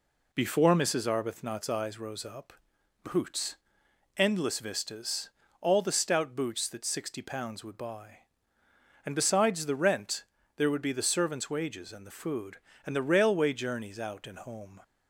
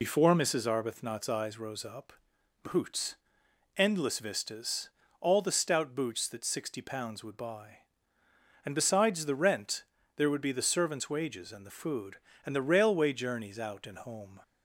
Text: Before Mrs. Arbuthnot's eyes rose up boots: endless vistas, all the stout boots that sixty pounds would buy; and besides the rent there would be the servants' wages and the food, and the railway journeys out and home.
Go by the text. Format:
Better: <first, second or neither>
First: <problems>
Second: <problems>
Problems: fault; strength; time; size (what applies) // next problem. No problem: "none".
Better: first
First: pauses between "up" and "boots"; noticeable; at 2.5 s; 0.50 s long // pauses between "rent" and "there"; slight; at 10.2 s; 0.32 s long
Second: loses the start of "Before"; at 0.0 s; 75 ms // pauses between "up" and "boots"; noticeable; at 2.1 s; 0.50 s long // pauses between "rent" and "there"; slight; at 9.8 s; 0.32 s long